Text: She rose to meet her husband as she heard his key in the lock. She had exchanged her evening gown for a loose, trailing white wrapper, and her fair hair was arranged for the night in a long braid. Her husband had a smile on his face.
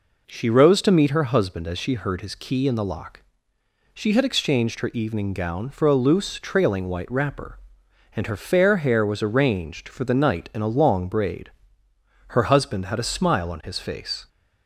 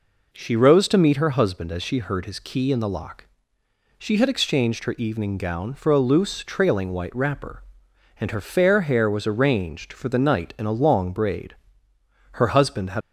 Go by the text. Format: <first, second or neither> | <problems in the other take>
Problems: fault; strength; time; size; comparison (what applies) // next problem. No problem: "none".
first | stops before "a smile on his face"; at 13.0 s